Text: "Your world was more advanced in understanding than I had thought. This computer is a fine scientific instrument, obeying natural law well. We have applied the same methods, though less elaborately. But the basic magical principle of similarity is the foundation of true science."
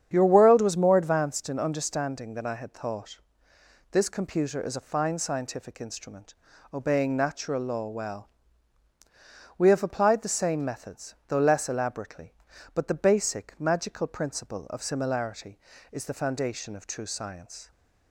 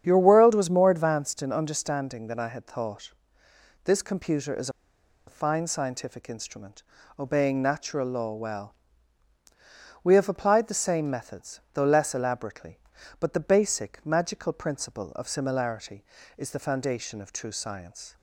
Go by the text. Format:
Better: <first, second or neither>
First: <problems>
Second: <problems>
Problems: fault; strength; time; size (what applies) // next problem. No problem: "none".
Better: first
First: starts louder than the rest; strong; until 1.1 s; 8.5 dB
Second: starts louder than the rest; strong; until 1.0 s; 8.5 dB // pauses between "is" and "a"; noticeable; at 4.6 s; 0.57 s long